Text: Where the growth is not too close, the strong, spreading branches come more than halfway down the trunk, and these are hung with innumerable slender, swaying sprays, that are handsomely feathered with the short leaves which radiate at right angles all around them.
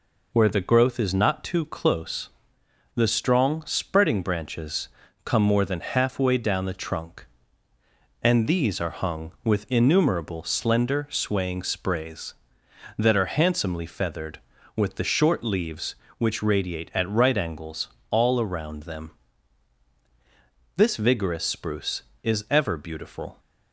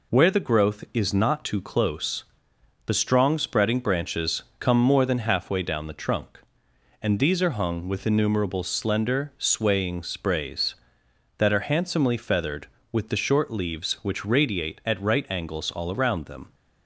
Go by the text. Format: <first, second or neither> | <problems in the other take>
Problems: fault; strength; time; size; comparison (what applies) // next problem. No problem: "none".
second | pauses between "branches" and "come"; slight; at 4.8 s; 0.34 s long; slight in the second // pauses between "angles" and "all"; slight; at 17.8 s; 0.24 s long // goes on to say "This vigorous spruce is ever beautiful"; strong; from 20.7 s on; 2.6 s long